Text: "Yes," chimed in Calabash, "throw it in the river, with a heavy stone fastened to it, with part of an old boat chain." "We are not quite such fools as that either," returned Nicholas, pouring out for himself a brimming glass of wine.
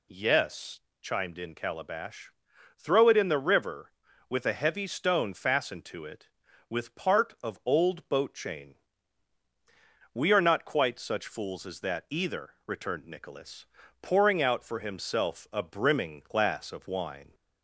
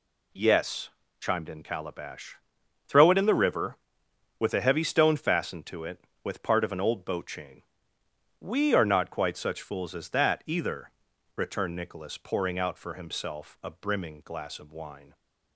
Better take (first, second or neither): second